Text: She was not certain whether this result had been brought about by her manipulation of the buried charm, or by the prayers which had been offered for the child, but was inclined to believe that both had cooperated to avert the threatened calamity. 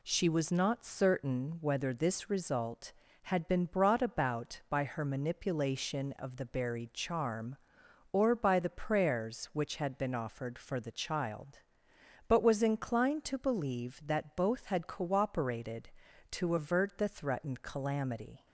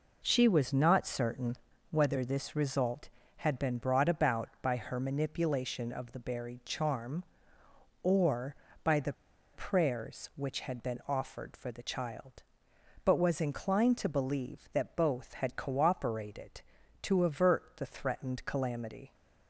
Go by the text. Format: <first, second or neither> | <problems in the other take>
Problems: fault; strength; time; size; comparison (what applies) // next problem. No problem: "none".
first | pauses between "certain" and "whether"; slight; at 1.5 s; 0.34 s long // pauses between "the" and "prayers"; at 9.1 s; 0.41 s long